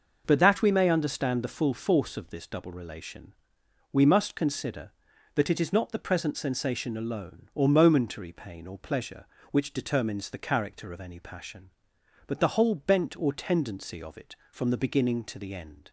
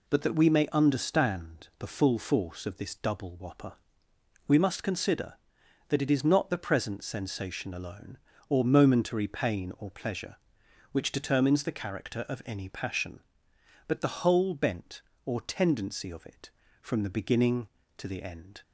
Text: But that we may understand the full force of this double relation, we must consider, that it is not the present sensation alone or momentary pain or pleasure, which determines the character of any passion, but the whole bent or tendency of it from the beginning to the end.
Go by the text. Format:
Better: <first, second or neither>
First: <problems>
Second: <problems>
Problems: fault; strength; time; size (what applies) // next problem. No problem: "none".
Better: first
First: none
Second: says "whopper" for "relation"; at 3.3 s